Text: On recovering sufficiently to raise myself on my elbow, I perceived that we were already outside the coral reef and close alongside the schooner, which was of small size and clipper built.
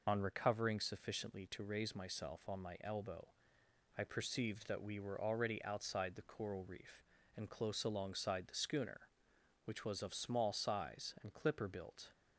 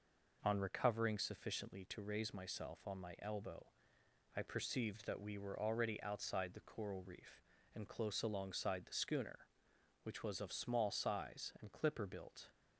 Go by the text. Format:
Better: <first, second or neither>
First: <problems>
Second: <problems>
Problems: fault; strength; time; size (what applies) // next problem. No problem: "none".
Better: second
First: loses the start of "On"; at 0.0 s; 35 ms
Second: none